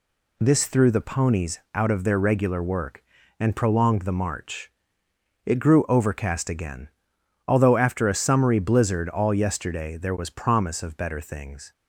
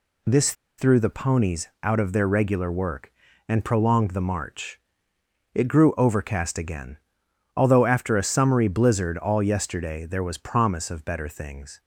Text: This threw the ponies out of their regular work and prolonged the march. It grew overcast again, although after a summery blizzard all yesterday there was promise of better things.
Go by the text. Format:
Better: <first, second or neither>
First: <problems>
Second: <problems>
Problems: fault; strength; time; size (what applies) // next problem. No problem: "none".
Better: first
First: none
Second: pauses between "This" and "threw"; slight; at 0.5 s; 0.25 s long